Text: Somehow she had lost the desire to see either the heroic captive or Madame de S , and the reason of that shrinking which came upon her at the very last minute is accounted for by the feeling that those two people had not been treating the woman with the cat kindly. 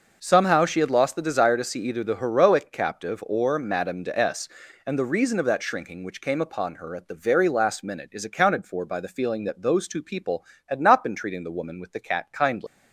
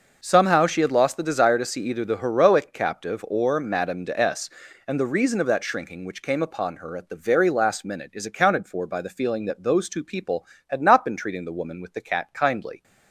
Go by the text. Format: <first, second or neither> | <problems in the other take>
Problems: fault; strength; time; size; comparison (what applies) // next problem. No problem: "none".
second | leaves "kindly" unfinished; at 12.6 s; 150 ms